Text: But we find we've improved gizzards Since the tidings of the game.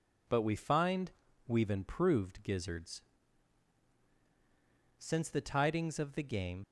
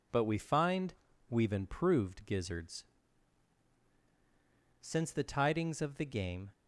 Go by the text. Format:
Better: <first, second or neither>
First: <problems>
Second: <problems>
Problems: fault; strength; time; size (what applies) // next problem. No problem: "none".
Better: second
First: pauses between "find" and "we've"; slight; at 1.1 s; 0.36 s long // pauses between "gizzards" and "Since"; strong; at 3.0 s; 1.9 s long // leaves "game" unfinished; at 6.6 s; 50 ms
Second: pauses between "find" and "we've"; slight; at 0.9 s; 0.36 s long // pauses between "gizzards" and "Since"; strong; at 2.8 s; 1.9 s long